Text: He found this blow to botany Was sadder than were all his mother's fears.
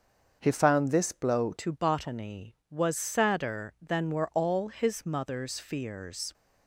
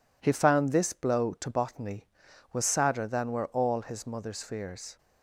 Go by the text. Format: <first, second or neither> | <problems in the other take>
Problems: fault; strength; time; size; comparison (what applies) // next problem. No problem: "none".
second | starts louder than the rest; until 1.4 s; 6.5 dB // changes voice at "to"; from 1.5 s on; 4.8 s long